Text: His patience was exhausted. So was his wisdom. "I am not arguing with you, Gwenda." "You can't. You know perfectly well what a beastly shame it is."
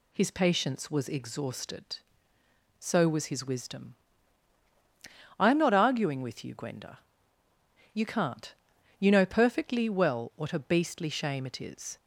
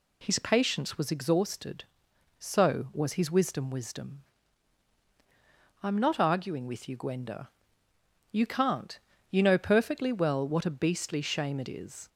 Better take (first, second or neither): first